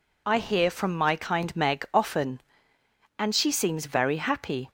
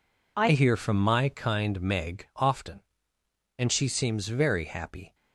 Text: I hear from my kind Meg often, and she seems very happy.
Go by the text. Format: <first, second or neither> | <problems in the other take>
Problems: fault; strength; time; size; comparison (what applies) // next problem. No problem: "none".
first | changes voice at "hear"; from 0.5 s on; 4.6 s long